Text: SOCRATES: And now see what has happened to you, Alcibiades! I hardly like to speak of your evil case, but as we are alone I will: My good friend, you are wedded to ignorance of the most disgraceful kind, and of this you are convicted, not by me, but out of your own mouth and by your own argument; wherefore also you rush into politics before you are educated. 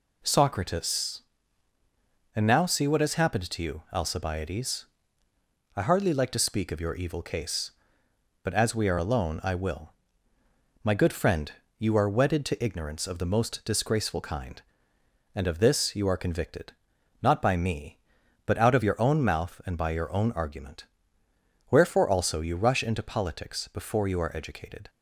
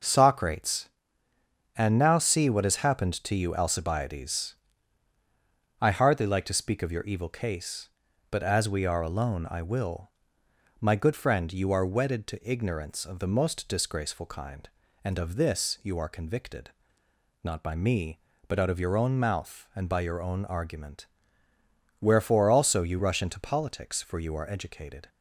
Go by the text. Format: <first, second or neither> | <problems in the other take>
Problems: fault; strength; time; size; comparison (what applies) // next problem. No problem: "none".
first | says "for" for "before"; at 24.0 s